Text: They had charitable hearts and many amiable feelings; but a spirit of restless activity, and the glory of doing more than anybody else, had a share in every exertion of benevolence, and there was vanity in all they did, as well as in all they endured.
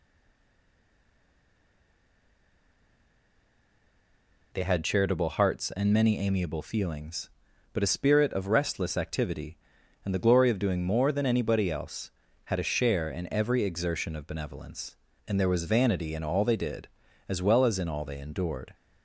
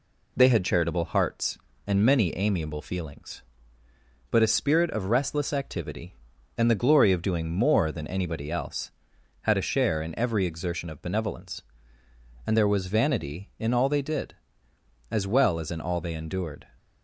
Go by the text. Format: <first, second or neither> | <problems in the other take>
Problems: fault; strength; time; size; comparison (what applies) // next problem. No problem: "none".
second | stays silent before the first word; strong; until 4.5 s; 4.5 s long